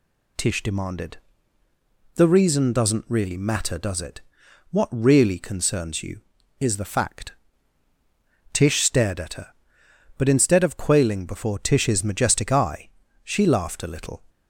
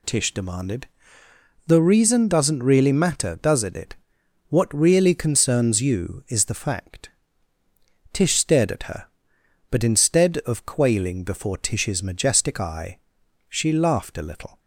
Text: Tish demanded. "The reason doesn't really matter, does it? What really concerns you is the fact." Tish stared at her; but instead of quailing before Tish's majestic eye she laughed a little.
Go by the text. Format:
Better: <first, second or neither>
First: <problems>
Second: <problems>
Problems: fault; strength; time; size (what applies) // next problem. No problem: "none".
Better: first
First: pauses between "eye" and "she"; slight; at 12.8 s; 0.34 s long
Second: says "it" twice; at 3.7 s // pauses between "eye" and "she"; noticeable; at 12.9 s; 0.50 s long